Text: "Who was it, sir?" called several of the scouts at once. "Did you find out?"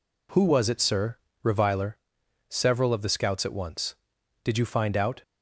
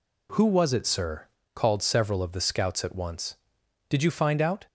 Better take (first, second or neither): second